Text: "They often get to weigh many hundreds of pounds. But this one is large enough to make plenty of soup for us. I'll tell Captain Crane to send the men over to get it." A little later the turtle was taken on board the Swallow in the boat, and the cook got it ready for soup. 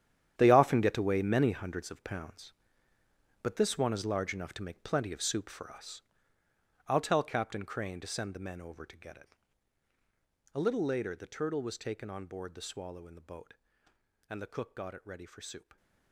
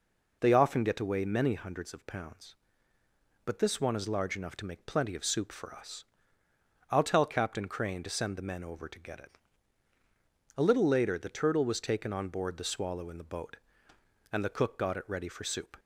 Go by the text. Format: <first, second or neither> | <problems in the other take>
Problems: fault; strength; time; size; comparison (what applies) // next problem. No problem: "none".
second | gets quieter; strong; throughout; 13.5 dB